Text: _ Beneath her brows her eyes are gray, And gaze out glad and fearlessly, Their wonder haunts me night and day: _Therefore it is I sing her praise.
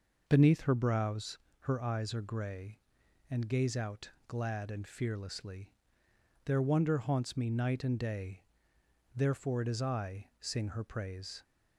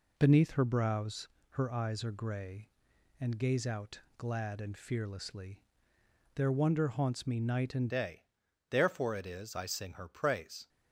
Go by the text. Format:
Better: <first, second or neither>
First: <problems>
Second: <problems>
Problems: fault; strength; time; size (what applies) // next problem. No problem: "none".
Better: first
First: pauses between "brows" and "her"; slight; at 1.3 s; 0.22 s long // pauses between "out" and "glad"; slight; at 4.1 s; 0.16 s long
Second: pauses between "brows" and "her"; slight; at 1.2 s; 0.22 s long // pauses between "out" and "glad"; slight; at 4.0 s; 0.16 s long // changes voice at "day"; from 7.9 s on; 2.7 s long